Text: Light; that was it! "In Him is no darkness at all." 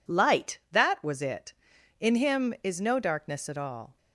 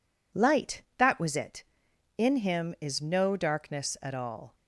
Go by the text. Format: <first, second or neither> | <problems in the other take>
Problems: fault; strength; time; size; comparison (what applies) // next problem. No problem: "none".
neither | none